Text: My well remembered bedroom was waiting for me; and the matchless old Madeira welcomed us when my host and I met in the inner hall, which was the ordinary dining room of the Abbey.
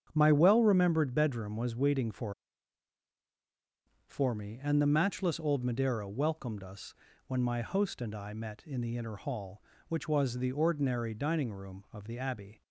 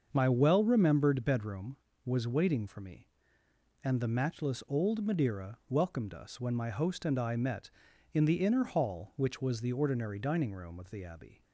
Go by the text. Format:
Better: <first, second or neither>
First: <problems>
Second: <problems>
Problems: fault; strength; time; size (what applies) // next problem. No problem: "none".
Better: second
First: starts louder than the rest; strong; until 1.1 s; 8 dB // says "for" twice; at 4.0 s // pauses between "us" and "when"; slight; at 6.9 s; 0.32 s long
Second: starts louder than the rest; until 1.1 s; 6.5 dB